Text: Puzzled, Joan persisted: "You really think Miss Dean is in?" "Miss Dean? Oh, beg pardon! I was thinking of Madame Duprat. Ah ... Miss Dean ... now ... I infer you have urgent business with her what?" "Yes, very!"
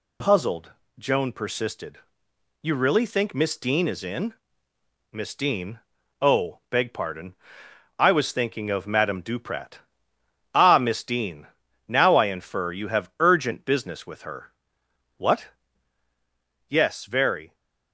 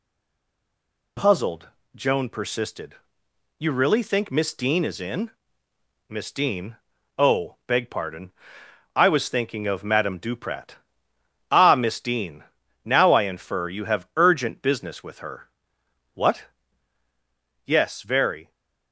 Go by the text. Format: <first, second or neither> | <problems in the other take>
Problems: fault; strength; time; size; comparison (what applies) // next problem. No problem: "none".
first | stays silent before the first word; until 1.1 s; 1.1 s long // pauses between "her" and "what"; noticeable; at 15.4 s; 0.64 s long; noticeable in the first